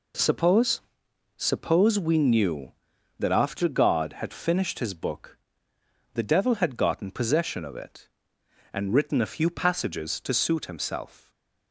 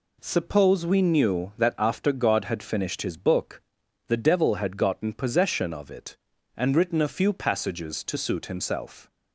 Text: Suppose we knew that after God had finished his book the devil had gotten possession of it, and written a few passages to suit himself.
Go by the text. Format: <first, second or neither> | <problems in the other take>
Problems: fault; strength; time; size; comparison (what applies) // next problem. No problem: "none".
second | says "Suppose" twice; at 1.3 s // pauses between "book" and "the"; noticeable; at 5.3 s; 0.78 s long; noticeable in the second // stays silent after the last word; slight; from 11.2 s on; 0.5 s long